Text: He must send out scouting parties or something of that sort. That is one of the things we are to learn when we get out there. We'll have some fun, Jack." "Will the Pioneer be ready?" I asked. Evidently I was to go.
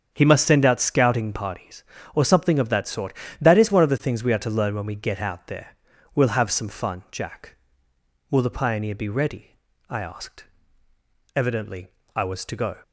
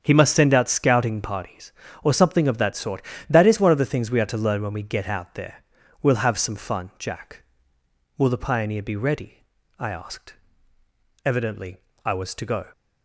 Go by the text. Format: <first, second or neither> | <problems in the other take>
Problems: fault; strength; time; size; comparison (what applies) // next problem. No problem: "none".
neither | starts louder than the rest; strong; the same in both // pauses between "Evidently" and "I"; slight; the same in both